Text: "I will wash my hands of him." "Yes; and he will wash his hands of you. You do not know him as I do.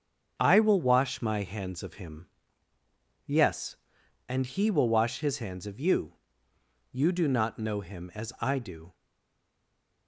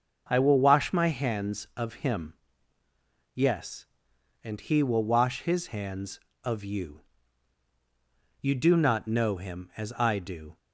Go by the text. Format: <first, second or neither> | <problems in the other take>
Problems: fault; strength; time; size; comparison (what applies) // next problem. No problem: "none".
second | starts louder than the rest; until 1.3 s; 7 dB; also in the second // stays silent after the last word; from 8.9 s on; 1.1 s long